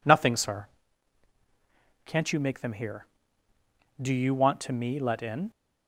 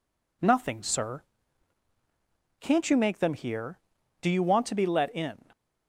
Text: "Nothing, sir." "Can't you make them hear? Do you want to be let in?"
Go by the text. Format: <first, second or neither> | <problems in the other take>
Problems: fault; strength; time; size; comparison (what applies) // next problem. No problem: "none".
second | says "me" for "be"; at 4.7 s